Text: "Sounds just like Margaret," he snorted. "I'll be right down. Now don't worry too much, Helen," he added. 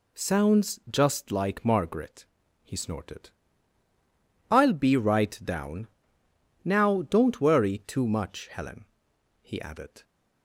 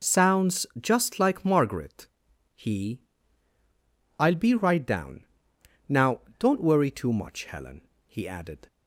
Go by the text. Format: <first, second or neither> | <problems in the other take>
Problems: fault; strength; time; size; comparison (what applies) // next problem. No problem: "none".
first | skips "snorted"; at 3.5 s // pauses between "Now" and "don't"; slight; at 6.2 s; 0.16 s long